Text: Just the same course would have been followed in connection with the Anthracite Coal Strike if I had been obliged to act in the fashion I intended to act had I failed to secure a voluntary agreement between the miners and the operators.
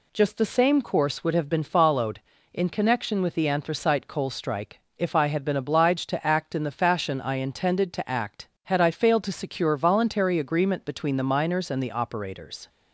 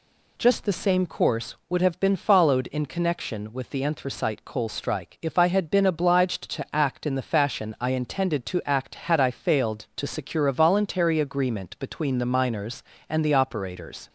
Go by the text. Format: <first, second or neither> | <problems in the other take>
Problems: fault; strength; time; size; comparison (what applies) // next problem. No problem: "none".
second | pauses between "Strike" and "if"; slight; at 4.7 s; 0.18 s long // skips "a"; at 9.7 s